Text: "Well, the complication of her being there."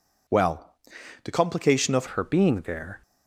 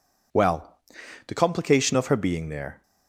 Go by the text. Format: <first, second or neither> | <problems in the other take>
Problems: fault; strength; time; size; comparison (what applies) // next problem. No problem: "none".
second | changes voice at "her"; from 2.0 s on; 1.0 s long